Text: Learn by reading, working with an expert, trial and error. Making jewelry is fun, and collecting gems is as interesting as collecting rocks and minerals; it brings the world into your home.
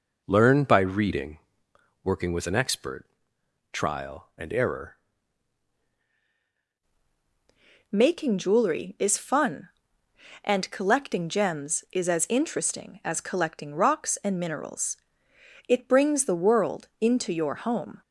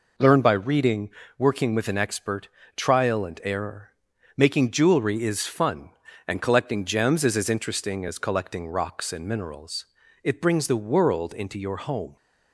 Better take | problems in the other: second | changes voice at "Making"; from 7.9 s on; 10.1 s long

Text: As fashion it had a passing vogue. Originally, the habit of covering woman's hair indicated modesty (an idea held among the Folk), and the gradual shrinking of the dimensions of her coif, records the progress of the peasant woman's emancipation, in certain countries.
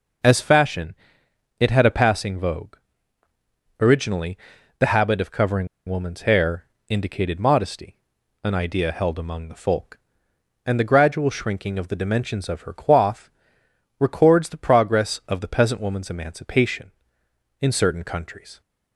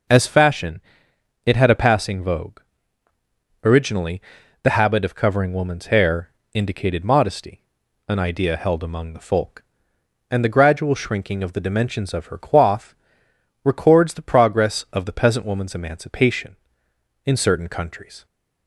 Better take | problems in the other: second | pauses between "fashion" and "it"; noticeable; at 0.9 s; 0.64 s long; noticeable in the second // pauses between "covering" and "woman's"; slight; at 5.6 s; 0.19 s long // pauses between "hair" and "indicated"; slight; at 6.6 s; 0.24 s long; slight in the second

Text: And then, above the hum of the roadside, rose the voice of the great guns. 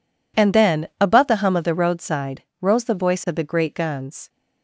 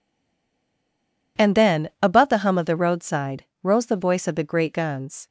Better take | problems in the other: first | stays silent before the first word; noticeable; until 1.3 s; 1.3 s long

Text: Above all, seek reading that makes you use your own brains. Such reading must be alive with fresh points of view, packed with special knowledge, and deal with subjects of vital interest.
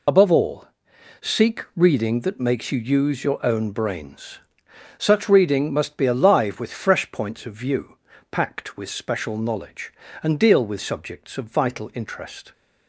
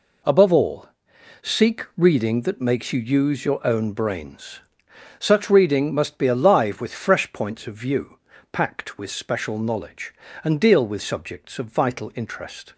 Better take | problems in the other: second | loses the start of "Above"; at 0.0 s; 40 ms

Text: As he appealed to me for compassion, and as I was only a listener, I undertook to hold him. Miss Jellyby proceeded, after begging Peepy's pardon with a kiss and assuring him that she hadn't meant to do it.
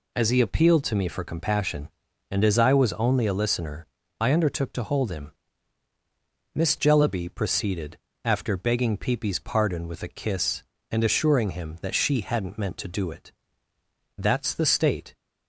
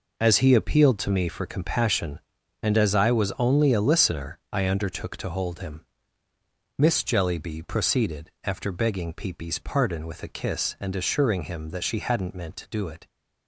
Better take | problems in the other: second | goes on to say "That's the state"; noticeable; from 14.1 s on; 0.98 s long

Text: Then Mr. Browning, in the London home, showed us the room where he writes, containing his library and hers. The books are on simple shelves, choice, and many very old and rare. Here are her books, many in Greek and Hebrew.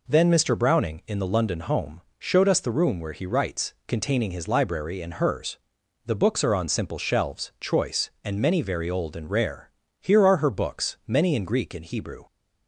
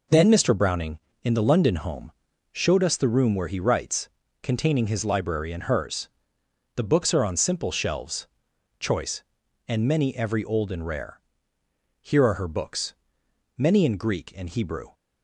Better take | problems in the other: first | says "every" for "very"; at 10.1 s

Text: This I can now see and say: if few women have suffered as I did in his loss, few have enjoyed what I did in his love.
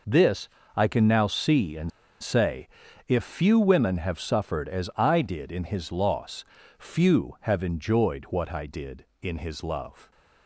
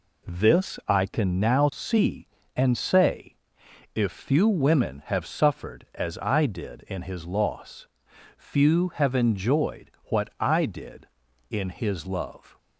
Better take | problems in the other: second | pauses between "This" and "I"; slight; at 0.4 s; 0.28 s long // pauses between "and" and "say"; slight; at 1.9 s; 0.32 s long

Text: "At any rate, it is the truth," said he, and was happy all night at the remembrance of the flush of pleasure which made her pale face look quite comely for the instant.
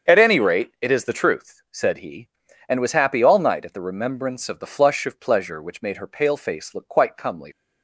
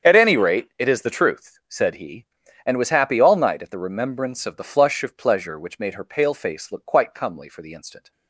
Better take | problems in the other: second | starts louder than the rest; strong; until 1.1 s; 7 dB; strong in the second // stops before "for the instant"; at 7.5 s

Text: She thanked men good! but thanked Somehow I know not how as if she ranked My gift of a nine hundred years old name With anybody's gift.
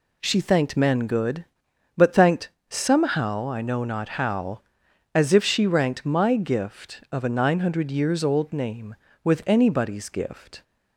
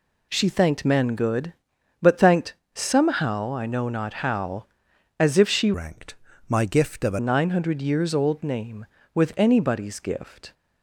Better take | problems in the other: first | pauses between "thanked" and "Somehow"; slight; at 2.5 s; 0.18 s long; slight in the first // changes voice from "ranked" to "a"; from 5.7 to 7.1 s; 1.4 s long // pauses between "ranked" and "My"; slight; at 6.1 s; 0.34 s long

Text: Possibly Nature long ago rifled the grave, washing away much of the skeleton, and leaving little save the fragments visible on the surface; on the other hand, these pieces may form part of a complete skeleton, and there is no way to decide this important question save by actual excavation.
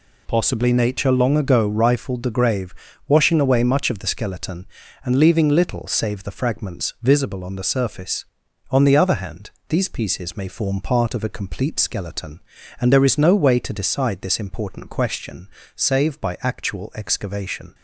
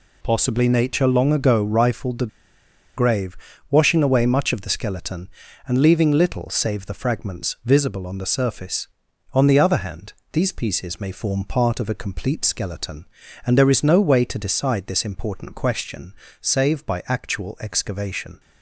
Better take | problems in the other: first | pauses between "the" and "grave"; noticeable; at 2.2 s; 0.69 s long // pauses between "question" and "save"; slight; at 16.1 s; 0.26 s long; slight in the first

